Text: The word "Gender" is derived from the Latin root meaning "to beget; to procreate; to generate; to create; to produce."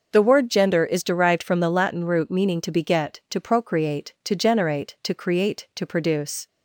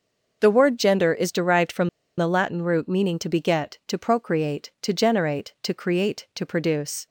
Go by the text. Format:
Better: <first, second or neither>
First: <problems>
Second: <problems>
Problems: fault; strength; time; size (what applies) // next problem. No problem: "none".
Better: first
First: none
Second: pauses between "from" and "the"; slight; at 1.8 s; 0.30 s long